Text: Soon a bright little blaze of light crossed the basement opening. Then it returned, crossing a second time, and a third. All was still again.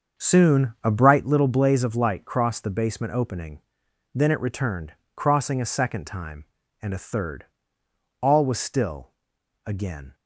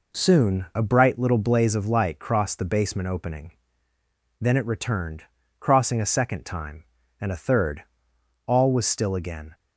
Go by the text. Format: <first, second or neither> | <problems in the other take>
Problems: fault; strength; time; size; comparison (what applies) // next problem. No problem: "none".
second | starts louder than the rest; until 1.4 s; 6.5 dB // pauses between "still" and "again"; noticeable; at 9.1 s; 0.56 s long